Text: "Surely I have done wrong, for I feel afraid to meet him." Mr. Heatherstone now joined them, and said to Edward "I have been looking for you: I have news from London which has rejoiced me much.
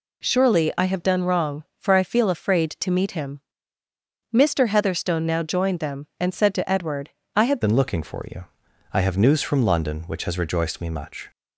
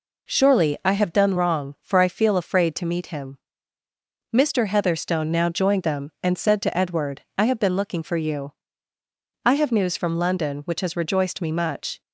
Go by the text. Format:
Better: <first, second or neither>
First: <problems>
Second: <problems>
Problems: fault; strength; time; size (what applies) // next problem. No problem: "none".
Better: second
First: pauses between "Edward" and "I"; slight; at 7.0 s; 0.26 s long // changes voice at "been"; from 7.6 s on; 3.7 s long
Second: pauses between "Edward" and "I"; slight; at 7.2 s; 0.16 s long